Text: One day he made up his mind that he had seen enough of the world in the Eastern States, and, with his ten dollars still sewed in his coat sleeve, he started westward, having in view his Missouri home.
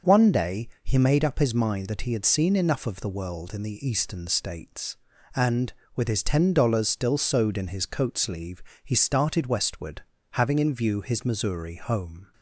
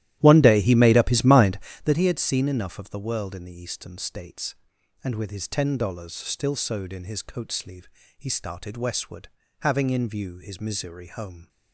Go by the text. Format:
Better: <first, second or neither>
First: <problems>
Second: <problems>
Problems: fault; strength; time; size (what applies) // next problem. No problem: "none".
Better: first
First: none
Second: starts louder than the rest; strong; until 2.0 s; 14 dB